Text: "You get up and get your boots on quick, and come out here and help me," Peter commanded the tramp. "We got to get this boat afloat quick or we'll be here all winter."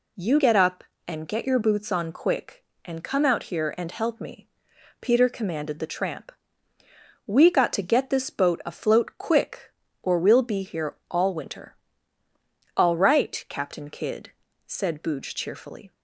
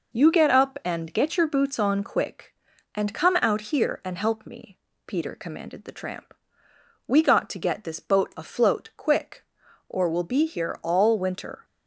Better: second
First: pauses between "here" and "all"; slight; at 10.9 s; 0.16 s long // goes on to say "All right Captain Kidd said Booge cheerfully"; strong; from 12.7 s on; 3.1 s long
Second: none

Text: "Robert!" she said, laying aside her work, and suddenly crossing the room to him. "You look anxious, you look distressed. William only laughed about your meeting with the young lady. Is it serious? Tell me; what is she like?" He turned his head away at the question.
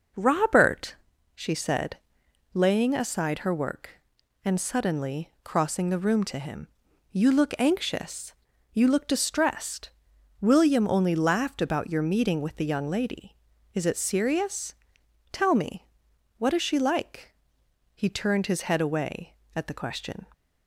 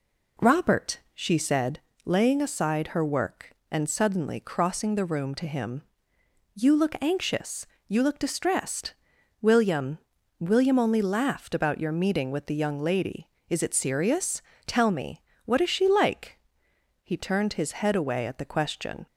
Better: first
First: none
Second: says "William" twice; at 10.3 s

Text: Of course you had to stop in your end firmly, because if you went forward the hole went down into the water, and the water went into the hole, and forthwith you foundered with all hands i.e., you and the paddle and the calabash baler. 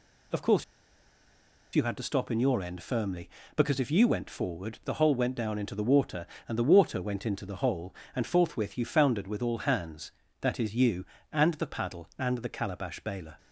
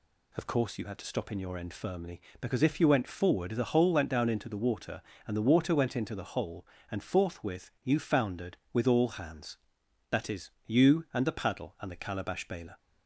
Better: second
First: pauses between "course" and "you"; at 0.6 s; 1.1 s long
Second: none

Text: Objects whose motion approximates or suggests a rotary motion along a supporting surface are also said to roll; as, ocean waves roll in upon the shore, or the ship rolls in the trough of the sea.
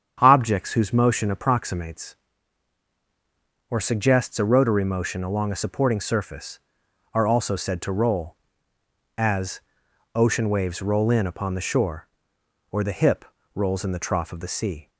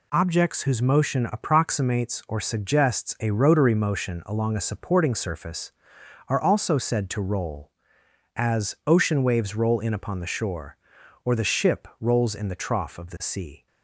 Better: second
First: starts louder than the rest; strong; until 1.2 s; 8 dB // says "hip" for "ship"; at 12.9 s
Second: none

